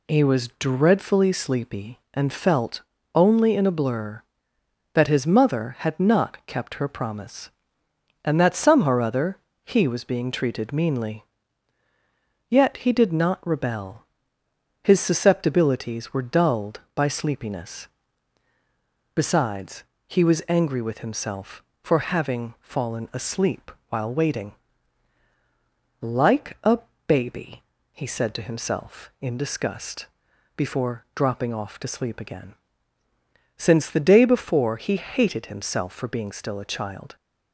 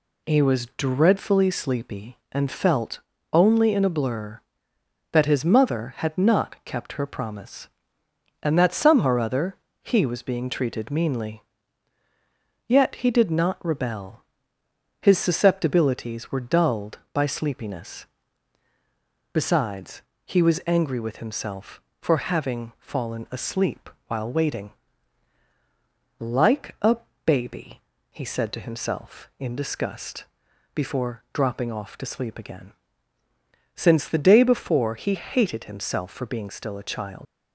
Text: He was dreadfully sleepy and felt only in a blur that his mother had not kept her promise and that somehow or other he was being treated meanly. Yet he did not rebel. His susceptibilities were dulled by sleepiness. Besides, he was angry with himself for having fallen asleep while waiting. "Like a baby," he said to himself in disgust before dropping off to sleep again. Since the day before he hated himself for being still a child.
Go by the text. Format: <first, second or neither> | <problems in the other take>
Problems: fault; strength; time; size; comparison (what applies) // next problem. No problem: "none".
first | pauses between "felt" and "only"; slight; at 2.9 s; 0.34 s long; slight in the first // pauses between "other" and "he"; slight; at 9.5 s; 0.26 s long; slight in the first // pauses between "asleep" and "while"; slight; at 23.8 s; 0.18 s long; slight in the first // pauses between "a" and "baby"; slight; at 26.9 s; 0.28 s long; slight in the first // pauses between "disgust" and "before"; noticeable; at 30.2 s; 0.48 s long; noticeable in the first // leaves "child" unfinished; at 37.2 s; 85 ms